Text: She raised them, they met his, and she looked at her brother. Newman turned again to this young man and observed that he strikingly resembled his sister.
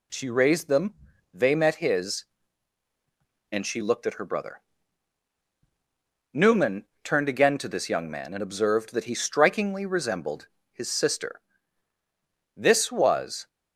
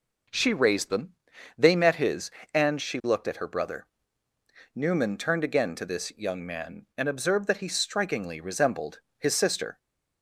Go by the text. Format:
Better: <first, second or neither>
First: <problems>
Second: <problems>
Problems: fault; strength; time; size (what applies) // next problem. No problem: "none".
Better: second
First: pauses between "Newman" and "turned"; slight; at 6.8 s; 0.18 s long // pauses between "resembled" and "his"; slight; at 10.4 s; 0.28 s long // goes on to say "This was"; noticeable; from 12.5 s on; 0.92 s long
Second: pauses between "resembled" and "his"; slight; at 9.0 s; 0.18 s long